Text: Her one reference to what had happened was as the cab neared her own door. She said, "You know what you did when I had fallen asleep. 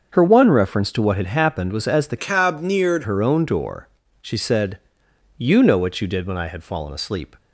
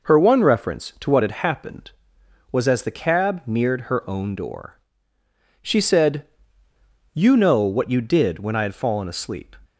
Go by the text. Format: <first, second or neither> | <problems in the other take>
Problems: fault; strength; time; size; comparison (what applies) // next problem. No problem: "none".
second | starts louder than the rest; until 1.1 s; 6.5 dB // changes voice from "cab" to "neared"; from 2.1 to 3.0 s; 0.9 s long